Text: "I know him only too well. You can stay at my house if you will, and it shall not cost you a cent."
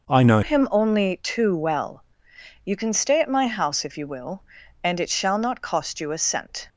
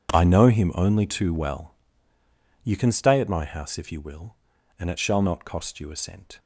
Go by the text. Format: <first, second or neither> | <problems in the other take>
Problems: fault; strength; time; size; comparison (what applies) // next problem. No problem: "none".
second | changes voice at "him"; from 0.4 s on; 6.2 s long